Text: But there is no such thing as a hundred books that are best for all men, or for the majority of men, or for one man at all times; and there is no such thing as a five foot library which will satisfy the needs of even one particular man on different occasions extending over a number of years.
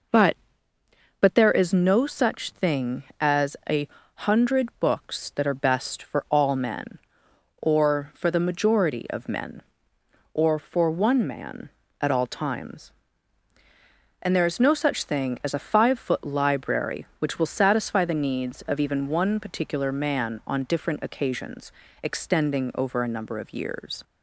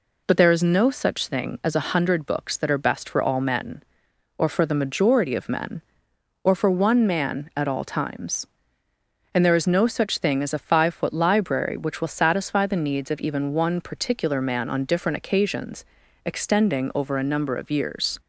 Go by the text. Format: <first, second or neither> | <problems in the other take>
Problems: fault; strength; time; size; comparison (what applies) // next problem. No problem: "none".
second | says "But" twice; at 1.1 s // pauses between "a" and "hundred"; slight; at 3.8 s; 0.26 s long // pauses between "occasions" and "extending"; slight; at 21.7 s; 0.32 s long; also in the second